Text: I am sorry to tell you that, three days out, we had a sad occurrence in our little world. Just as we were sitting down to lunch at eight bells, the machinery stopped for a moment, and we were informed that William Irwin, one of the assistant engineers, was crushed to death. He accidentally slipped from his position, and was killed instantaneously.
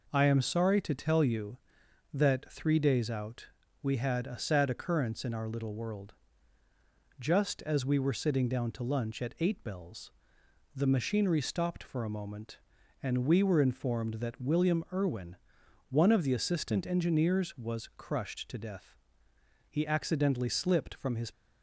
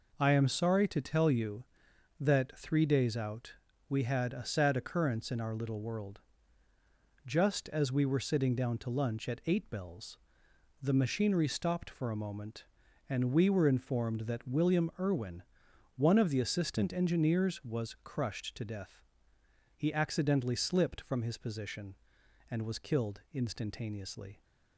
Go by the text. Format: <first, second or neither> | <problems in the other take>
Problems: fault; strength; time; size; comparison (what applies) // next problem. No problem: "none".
second | stops before "position and was killed instantaneously"; at 21.3 s